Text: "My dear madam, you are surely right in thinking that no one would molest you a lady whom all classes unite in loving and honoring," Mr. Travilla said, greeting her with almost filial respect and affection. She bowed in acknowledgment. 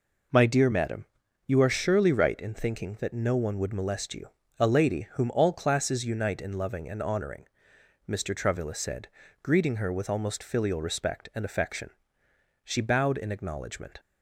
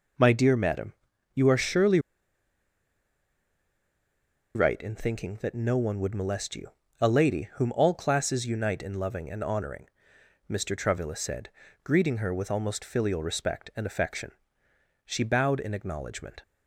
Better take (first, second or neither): first